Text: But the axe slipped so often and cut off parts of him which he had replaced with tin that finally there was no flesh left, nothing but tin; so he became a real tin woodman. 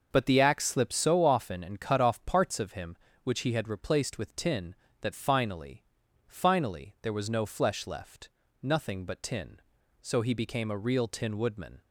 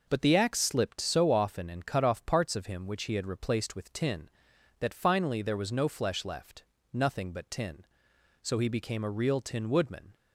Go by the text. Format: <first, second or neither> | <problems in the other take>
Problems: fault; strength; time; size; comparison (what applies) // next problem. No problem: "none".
second | starts louder than the rest; until 1.1 s; 6 dB // says "finally" twice; at 6.2 s